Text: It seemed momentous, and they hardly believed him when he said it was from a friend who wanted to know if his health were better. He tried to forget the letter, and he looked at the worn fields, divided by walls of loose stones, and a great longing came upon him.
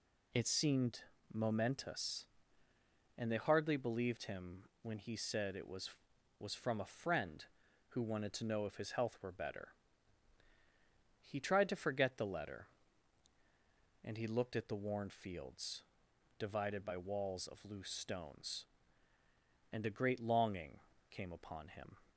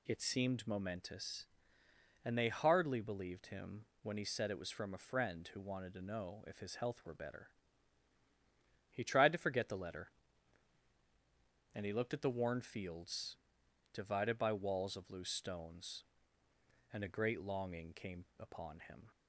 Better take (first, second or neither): second